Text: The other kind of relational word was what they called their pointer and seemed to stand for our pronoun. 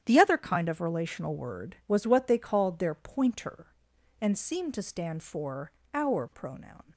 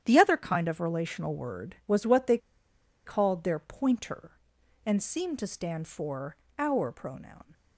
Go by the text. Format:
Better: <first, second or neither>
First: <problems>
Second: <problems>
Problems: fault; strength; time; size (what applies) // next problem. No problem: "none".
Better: first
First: starts louder than the rest; strong; until 1.0 s; 10 dB // pauses between "for" and "our"; slight; at 5.7 s; 0.24 s long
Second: starts louder than the rest; strong; until 1.0 s; 10 dB // pauses between "they" and "called"; noticeable; at 2.3 s; 0.68 s long // pauses between "for" and "our"; slight; at 6.3 s; 0.24 s long